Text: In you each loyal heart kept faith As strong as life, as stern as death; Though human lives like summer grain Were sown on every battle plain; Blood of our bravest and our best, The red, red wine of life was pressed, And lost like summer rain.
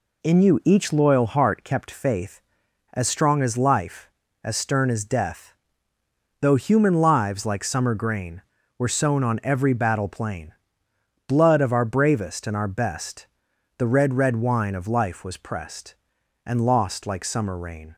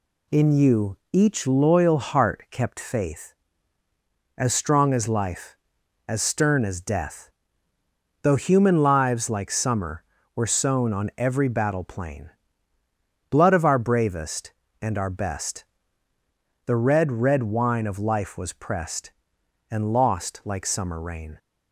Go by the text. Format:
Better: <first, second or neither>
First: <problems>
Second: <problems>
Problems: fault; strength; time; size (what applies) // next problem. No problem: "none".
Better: first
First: none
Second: skips "grain"; at 10.2 s